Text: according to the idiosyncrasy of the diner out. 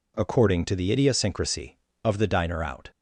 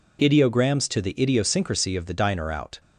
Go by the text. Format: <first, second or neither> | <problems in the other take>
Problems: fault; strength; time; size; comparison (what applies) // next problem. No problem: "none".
first | says "ideograms" for "according"; at 0.1 s